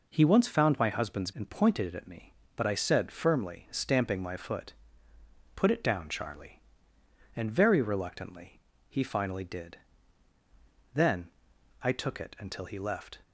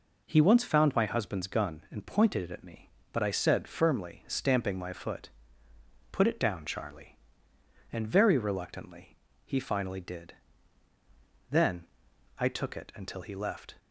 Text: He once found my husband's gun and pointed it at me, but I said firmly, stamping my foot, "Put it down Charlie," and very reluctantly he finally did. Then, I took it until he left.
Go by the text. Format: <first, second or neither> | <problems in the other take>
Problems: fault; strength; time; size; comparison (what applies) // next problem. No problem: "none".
second | skips "gun"; at 1.3 s // pauses between "reluctantly" and "he"; slight; at 8.6 s; 0.28 s long; slight in the second